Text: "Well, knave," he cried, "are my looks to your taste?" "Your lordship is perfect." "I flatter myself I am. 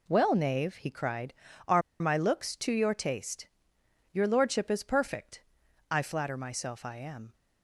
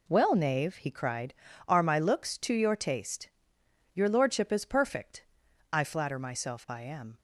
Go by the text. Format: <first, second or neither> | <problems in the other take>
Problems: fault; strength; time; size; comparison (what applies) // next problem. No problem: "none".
second | pauses between "are" and "my"; slight; at 1.8 s; 0.19 s long